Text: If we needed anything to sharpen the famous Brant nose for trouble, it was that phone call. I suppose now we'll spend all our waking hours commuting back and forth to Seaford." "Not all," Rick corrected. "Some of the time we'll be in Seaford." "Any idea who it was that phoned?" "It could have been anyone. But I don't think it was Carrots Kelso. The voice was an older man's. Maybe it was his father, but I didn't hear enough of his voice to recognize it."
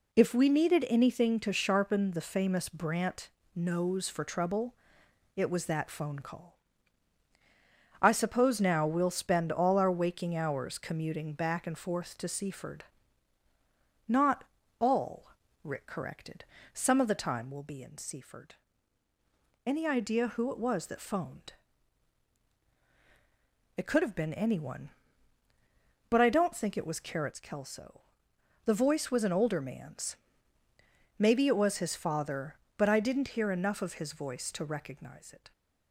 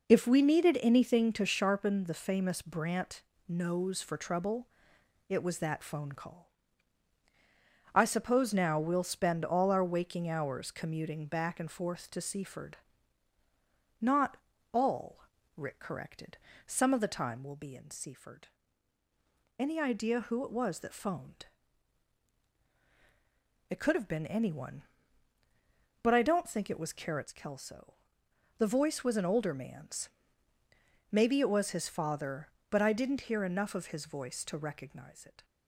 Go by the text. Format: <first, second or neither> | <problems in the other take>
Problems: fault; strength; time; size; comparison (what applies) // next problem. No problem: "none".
first | starts louder than the rest; noticeable; until 1.6 s; 4.5 dB // pauses between "Brant" and "nose"; slight; at 3.2 s; 0.26 s long; slight in the first // pauses between "Not" and "all"; slight; at 14.3 s; 0.36 s long; slight in the first